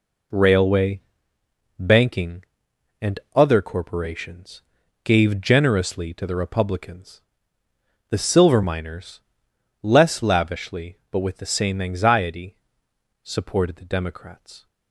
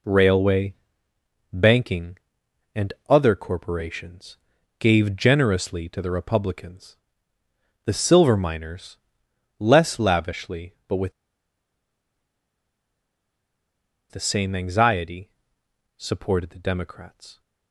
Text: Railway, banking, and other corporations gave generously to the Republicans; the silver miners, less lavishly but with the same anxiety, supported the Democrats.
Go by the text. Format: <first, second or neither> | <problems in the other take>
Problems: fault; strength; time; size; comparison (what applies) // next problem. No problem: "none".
first | pauses between "and" and "other"; slight; at 2.9 s; 0.16 s long; slight in the first // pauses between "corporations" and "gave"; at 4.3 s; 0.40 s long; also in the first // pauses between "with" and "the"; strong; at 11.1 s; 2.9 s long